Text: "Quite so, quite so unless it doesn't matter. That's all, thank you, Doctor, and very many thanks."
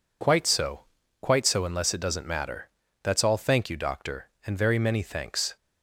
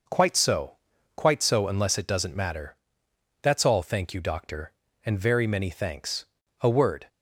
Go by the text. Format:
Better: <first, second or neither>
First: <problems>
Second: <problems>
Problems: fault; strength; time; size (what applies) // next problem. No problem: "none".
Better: first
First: none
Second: goes on to say "A word"; slight; from 6.5 s on; 0.48 s long